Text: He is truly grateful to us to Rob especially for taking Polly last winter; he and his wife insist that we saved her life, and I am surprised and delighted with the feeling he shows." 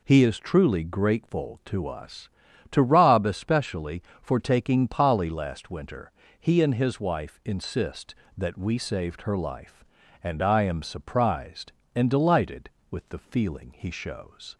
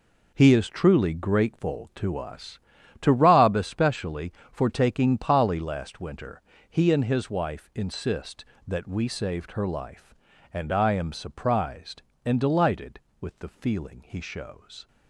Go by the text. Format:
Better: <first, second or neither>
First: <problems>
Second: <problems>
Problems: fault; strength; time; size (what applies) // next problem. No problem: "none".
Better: first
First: none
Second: gets quieter; strong; throughout; 10.5 dB